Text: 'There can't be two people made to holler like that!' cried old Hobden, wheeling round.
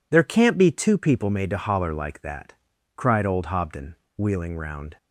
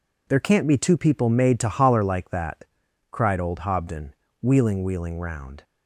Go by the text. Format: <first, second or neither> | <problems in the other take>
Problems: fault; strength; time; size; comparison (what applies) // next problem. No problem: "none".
first | says "wheeling" twice; at 4.8 s